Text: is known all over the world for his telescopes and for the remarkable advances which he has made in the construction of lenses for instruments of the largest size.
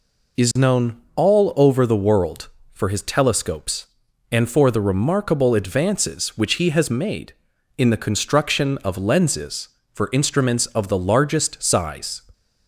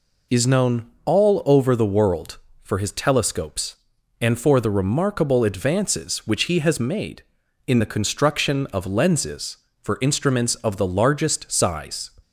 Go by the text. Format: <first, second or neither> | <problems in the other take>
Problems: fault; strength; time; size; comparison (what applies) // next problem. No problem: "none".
neither | pauses between "known" and "all"; slight; the same in both